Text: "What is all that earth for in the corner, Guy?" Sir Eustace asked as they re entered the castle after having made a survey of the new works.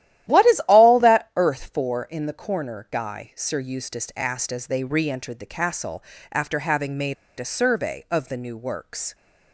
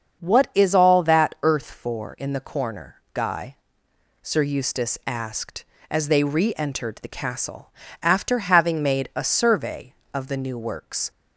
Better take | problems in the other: second | starts louder than the rest; strong; until 1.4 s; 13 dB; also in the second // pauses between "castle" and "after"; slight; at 6.0 s; 0.28 s long; slight in the second // pauses between "made" and "a"; slight; at 7.1 s; 0.23 s long

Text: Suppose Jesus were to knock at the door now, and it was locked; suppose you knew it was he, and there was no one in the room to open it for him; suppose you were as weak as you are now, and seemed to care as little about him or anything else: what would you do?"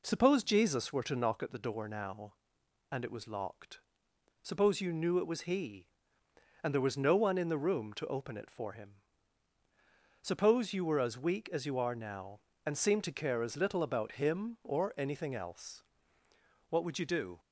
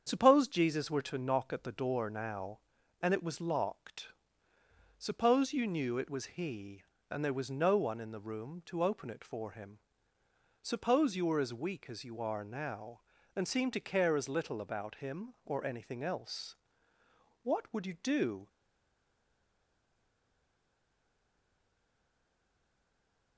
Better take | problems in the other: first | starts louder than the rest; strong; until 1.0 s; 7.5 dB // stays silent after the last word; strong; from 18.4 s on; 4.9 s long

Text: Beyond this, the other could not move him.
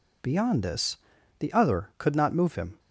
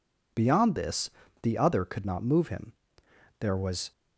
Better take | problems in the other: first | goes on to say "There was"; from 3.3 s on; 0.52 s long

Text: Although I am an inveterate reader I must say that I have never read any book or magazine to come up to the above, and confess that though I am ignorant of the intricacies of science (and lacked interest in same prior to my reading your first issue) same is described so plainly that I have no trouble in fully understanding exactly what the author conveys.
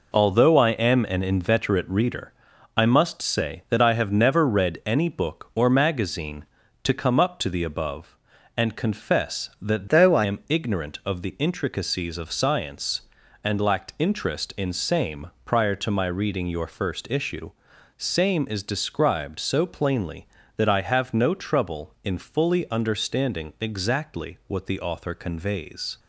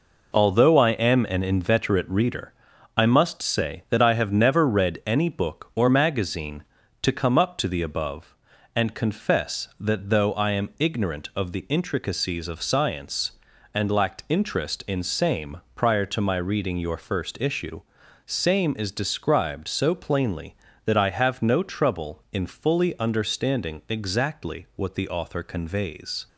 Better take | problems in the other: second | pauses between "reader" and "I"; at 2.3 s; 0.44 s long; also in the second // changes voice from "though" to "I"; from 9.8 to 10.2 s; 0.4 s long // pauses between "same" and "prior"; slight; at 15.2 s; 0.18 s long; slight in the second

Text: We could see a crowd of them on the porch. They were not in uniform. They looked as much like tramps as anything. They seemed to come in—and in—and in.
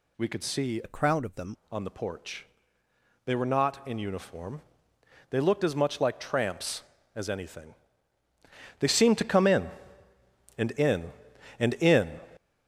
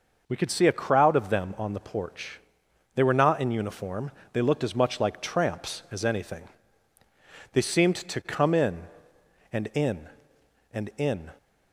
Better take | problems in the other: second | changes voice from "a" to "them"; from 0.8 to 1.5 s; 0.7 s long

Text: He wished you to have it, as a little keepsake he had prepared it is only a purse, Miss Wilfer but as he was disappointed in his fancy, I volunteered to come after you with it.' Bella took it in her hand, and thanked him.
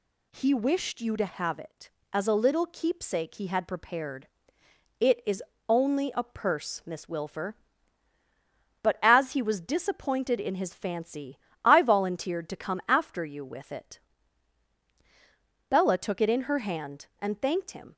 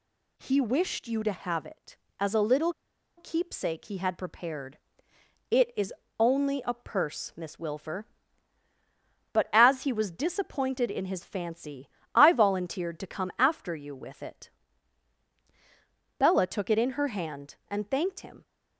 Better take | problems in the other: first | pauses between "little" and "keepsake"; at 2.7 s; 0.44 s long // pauses between "prepared" and "it"; noticeable; at 4.7 s; 0.74 s long; noticeable in the first // pauses between "is" and "only"; slight; at 5.9 s; 0.28 s long; slight in the first

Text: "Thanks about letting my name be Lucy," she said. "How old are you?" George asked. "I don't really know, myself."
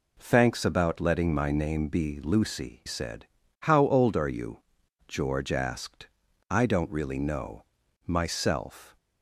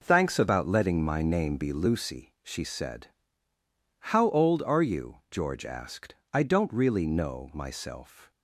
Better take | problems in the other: second | skips "she"; at 2.8 s

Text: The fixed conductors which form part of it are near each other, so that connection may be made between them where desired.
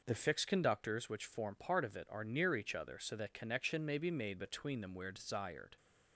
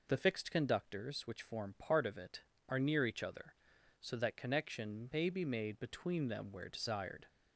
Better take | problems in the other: neither | none

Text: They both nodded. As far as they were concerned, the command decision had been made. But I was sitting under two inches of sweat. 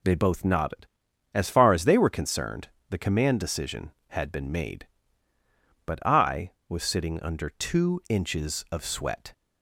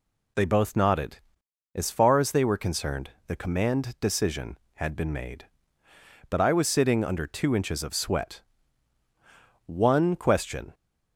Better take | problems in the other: first | goes on to say "One question"; noticeable; from 9.6 s on; 1.0 s long

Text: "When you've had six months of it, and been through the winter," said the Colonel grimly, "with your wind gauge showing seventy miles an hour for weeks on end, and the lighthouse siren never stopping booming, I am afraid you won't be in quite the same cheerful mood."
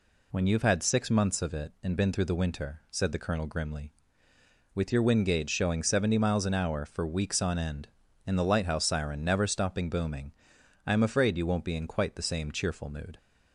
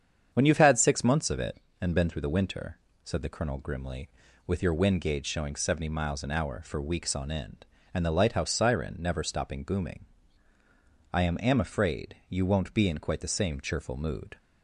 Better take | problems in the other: first | starts louder than the rest; strong; until 1.3 s; 8 dB // says "am" twice; at 11.3 s

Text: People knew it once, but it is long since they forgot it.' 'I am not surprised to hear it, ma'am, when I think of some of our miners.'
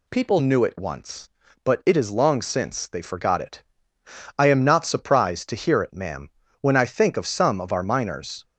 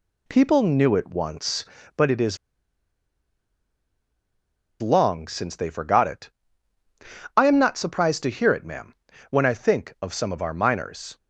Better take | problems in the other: first | pauses between "is" and "long"; strong; at 2.3 s; 2.4 s long

